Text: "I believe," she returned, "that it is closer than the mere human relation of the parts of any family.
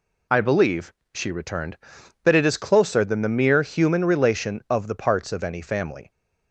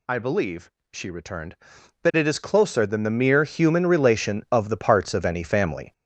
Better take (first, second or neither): first